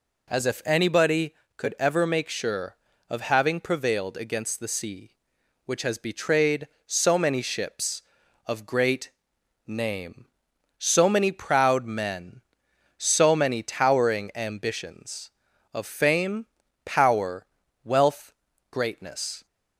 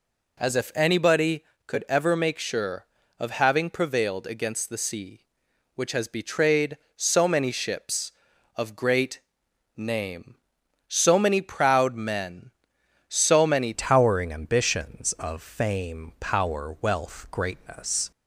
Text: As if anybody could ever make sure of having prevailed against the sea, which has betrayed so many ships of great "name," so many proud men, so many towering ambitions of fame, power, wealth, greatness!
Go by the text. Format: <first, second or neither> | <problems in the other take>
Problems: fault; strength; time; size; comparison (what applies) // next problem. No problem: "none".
first | pauses between "great" and "name"; noticeable; at 9.1 s; 0.56 s long; noticeable in the first // changes voice at "towering"; from 13.7 s on; 4.4 s long